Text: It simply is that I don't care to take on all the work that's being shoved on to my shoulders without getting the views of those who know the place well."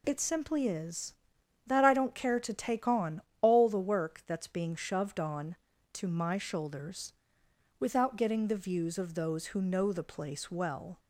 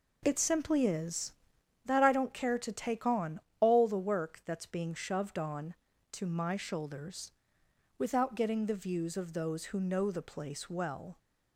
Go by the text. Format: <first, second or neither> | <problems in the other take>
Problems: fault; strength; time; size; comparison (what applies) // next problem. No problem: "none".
first | starts louder than the rest; noticeable; until 1.7 s; 4.5 dB // pauses between "on" and "all"; slight; at 3.3 s; 0.20 s long; slight in the first // pauses between "shoulders" and "without"; noticeable; at 7.3 s; 0.66 s long; noticeable in the first